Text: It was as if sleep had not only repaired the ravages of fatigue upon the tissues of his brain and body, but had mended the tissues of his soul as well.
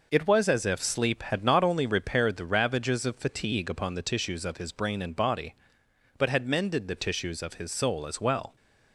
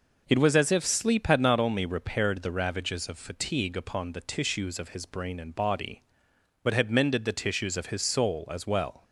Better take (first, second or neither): neither